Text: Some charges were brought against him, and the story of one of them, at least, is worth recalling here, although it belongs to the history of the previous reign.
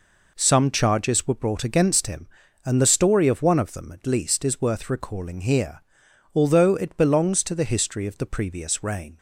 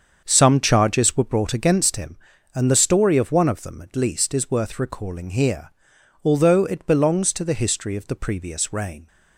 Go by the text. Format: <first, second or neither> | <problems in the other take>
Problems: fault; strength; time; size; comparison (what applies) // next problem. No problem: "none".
first | starts louder than the rest; until 1.7 s; 7 dB